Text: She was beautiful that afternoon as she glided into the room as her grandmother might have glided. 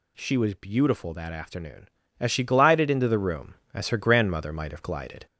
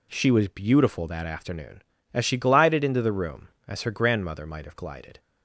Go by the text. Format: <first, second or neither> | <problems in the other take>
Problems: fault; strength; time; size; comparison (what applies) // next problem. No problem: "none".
second | gets louder; slight; throughout; 2 dB